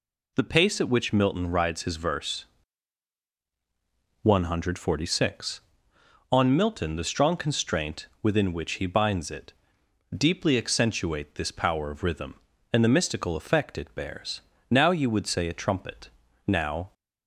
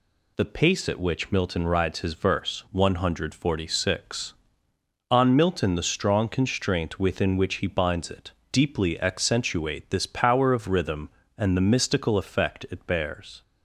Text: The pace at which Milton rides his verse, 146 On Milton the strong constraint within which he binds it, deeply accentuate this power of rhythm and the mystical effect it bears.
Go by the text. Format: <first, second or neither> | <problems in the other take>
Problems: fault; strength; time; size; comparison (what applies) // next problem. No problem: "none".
second | pauses between "constraint" and "within"; slight; at 8.0 s; 0.16 s long // goes on to say "Now you would say a trumpet now"; strong; from 14.7 s on; 2.2 s long